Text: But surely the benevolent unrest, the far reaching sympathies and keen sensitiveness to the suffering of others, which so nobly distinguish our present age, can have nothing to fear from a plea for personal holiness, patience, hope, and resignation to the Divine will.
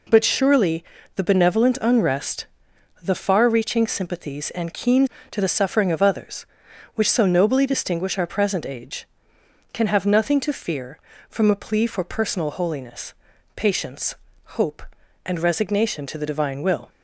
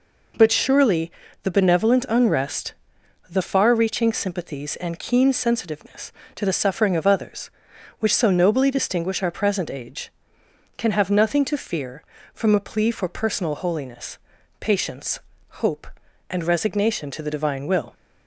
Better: second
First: pauses between "surely" and "the"; slight; at 0.8 s; 0.32 s long // skips "sensitiveness"; at 5.1 s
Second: pauses between "surely" and "the"; slight; at 1.1 s; 0.32 s long

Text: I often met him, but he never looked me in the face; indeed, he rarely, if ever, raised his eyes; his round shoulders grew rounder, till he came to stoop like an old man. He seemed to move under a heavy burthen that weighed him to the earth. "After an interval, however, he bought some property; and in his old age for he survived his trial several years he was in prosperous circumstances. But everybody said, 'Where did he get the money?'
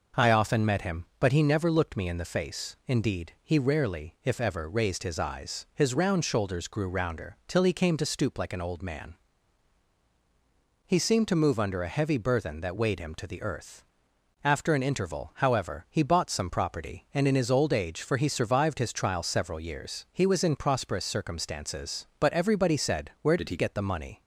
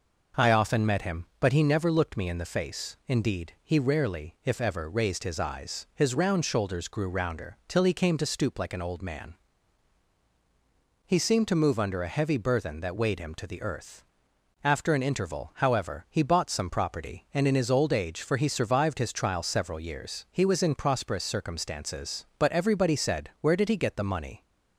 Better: second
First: changes voice from "did" to "he"; from 23.3 to 23.5 s; 0.2 s long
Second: none

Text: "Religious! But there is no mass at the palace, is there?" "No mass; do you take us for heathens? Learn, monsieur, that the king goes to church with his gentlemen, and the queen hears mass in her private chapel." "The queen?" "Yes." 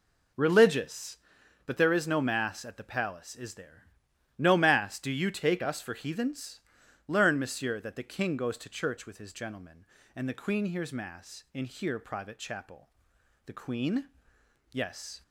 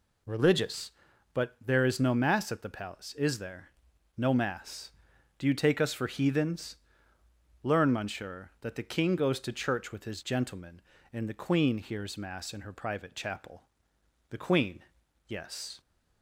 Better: second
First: says "here" for "her"; at 11.6 s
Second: none

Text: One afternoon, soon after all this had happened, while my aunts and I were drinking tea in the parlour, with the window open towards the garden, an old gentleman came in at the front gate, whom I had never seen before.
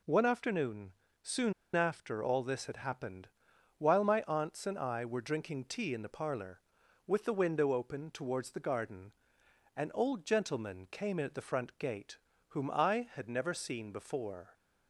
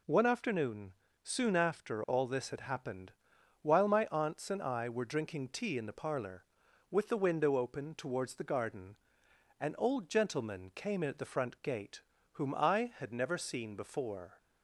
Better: second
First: pauses between "soon" and "after"; slight; at 1.5 s; 0.22 s long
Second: none

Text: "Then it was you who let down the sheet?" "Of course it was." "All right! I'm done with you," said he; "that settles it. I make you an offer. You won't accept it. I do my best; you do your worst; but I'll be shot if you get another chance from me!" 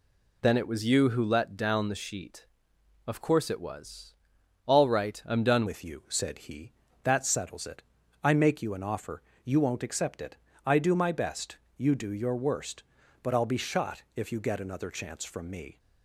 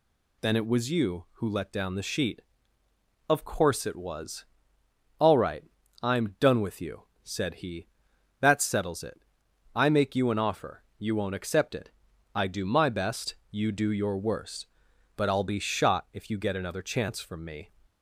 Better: second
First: changes voice at "with"; from 5.6 s on; 10.1 s long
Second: none

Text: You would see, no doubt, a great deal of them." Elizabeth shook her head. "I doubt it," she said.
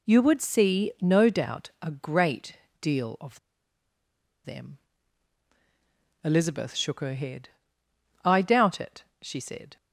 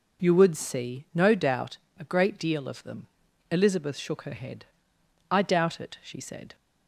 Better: second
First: pauses between "great" and "deal"; slight; at 2.5 s; 0.24 s long // pauses between "of" and "them"; at 3.3 s; 1.0 s long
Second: none

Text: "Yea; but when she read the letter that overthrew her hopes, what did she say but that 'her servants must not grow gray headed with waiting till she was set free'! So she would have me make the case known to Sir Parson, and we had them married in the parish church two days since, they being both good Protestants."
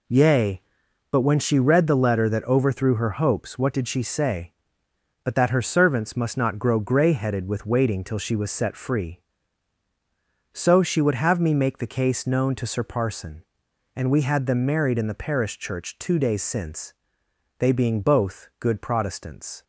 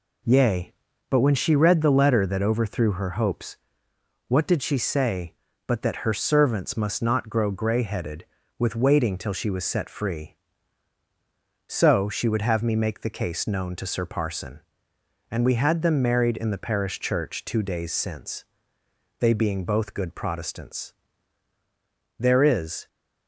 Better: first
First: none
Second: goes on to say "There is"; noticeable; from 22.1 s on; 0.70 s long

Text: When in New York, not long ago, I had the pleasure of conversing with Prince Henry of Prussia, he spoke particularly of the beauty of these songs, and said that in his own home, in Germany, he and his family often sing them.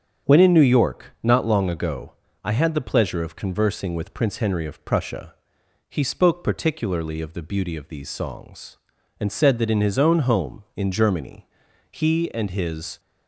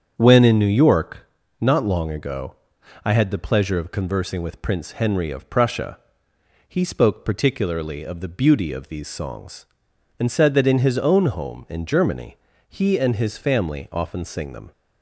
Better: second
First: starts louder than the rest; strong; until 1.3 s; 7.5 dB // stops before "family often sing them"; at 12.9 s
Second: starts louder than the rest; strong; until 1.1 s; 8 dB

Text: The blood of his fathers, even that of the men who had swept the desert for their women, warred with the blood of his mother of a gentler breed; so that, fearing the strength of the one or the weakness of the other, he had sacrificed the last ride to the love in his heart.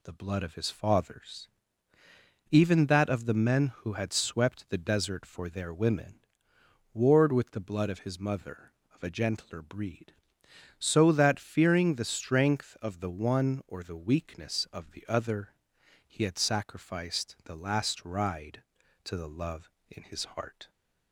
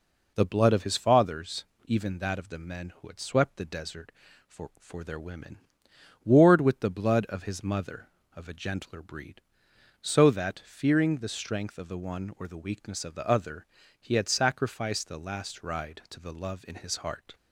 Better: first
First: none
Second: says "for" twice; at 4.7 s

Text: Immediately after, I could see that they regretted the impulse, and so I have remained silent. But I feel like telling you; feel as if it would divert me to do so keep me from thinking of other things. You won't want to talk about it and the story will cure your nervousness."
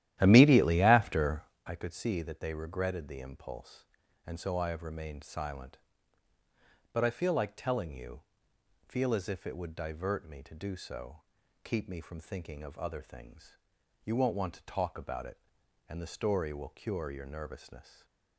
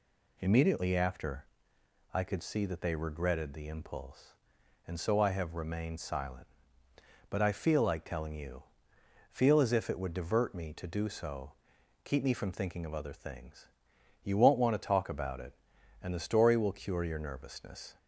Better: second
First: starts louder than the rest; strong; until 1.7 s; 12.5 dB // pauses between "so" and "keep"; at 11.2 s; 0.44 s long // stays silent after the last word; slight; from 17.8 s on; 0.5 s long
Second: pauses between "so" and "keep"; noticeable; at 11.5 s; 0.50 s long

